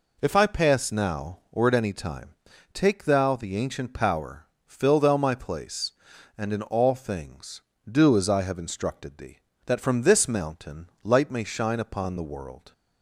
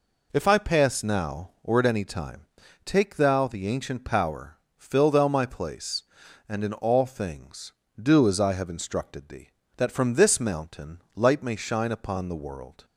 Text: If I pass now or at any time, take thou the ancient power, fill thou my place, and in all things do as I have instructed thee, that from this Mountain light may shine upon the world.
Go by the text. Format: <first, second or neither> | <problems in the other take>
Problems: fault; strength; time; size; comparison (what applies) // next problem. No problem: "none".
neither | none